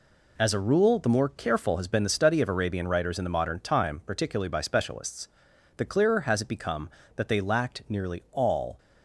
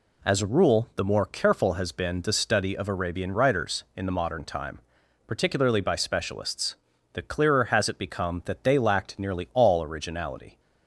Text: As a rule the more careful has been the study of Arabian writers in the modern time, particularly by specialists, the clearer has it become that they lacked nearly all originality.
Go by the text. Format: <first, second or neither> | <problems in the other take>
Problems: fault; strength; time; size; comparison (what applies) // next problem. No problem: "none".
second | stops before "originality"; at 8.7 s